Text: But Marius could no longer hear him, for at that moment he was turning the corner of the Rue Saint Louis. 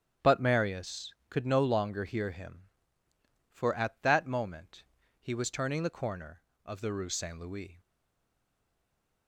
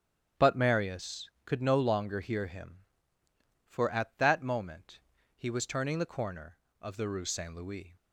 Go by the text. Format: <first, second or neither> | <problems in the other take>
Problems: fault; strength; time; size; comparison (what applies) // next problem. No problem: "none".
second | starts louder than the rest; strong; until 1.3 s; 9.5 dB; strong in the second // pauses between "moment" and "he"; slight; at 4.8 s; 0.34 s long; slight in the second // stays silent after the last word; noticeable; from 7.7 s on; 1.5 s long